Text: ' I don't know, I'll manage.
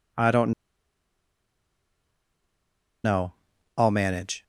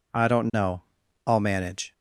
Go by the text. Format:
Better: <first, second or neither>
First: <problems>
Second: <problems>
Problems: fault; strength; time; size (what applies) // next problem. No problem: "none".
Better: second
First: pauses between "don't" and "know"; strong; at 0.5 s; 2.5 s long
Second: none